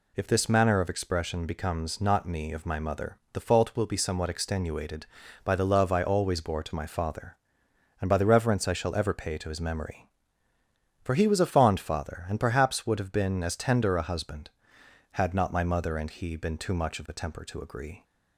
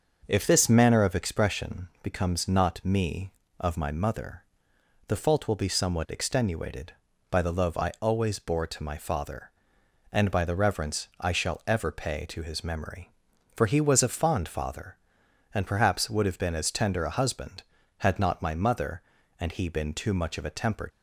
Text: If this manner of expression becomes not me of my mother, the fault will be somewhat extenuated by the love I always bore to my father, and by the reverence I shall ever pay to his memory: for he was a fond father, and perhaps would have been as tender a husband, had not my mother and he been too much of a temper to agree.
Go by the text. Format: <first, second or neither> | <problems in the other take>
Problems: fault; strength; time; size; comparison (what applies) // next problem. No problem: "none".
first | starts louder than the rest; until 1.2 s; 6 dB // stops before "to agree"; at 20.9 s